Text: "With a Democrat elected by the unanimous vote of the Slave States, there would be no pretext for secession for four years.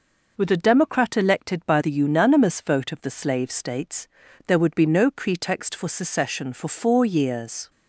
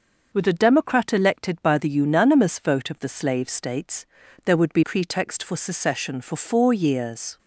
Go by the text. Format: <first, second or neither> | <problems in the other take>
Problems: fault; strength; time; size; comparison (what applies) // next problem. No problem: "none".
first | starts louder than the rest; noticeable; until 1.3 s; 6 dB // skips "no"; at 4.8 s